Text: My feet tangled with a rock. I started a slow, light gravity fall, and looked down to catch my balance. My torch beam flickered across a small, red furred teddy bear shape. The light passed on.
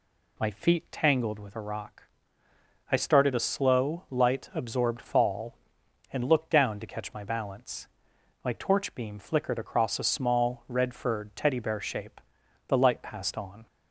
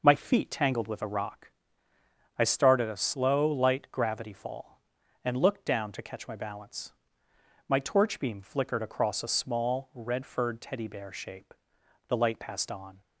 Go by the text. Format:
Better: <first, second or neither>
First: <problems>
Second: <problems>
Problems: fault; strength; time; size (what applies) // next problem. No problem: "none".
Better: second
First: says "absorbed" for "gravity"; at 4.5 s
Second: none